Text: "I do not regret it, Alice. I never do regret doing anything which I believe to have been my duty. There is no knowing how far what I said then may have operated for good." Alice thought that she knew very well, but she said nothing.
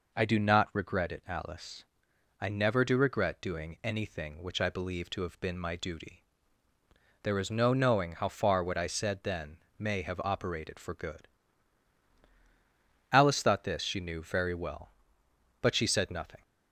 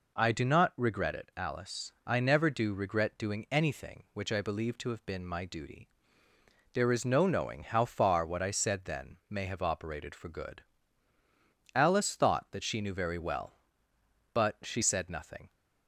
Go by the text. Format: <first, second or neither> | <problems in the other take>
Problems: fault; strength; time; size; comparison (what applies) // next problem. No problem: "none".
second | pauses between "then" and "may"; slight; at 9.5 s; 0.20 s long // says "this" for "that"; at 13.6 s